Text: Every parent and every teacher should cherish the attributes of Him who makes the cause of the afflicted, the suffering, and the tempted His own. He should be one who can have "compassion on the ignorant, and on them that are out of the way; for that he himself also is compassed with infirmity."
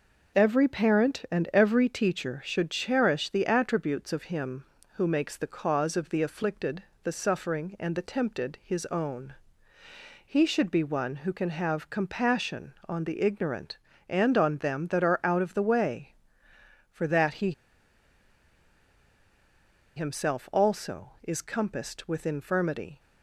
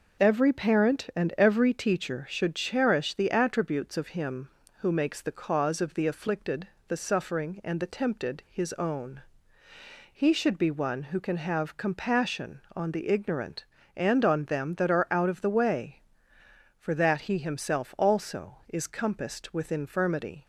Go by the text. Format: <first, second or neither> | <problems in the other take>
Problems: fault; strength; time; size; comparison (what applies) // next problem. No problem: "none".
second | pauses between "he" and "himself"; strong; at 17.5 s; 2.4 s long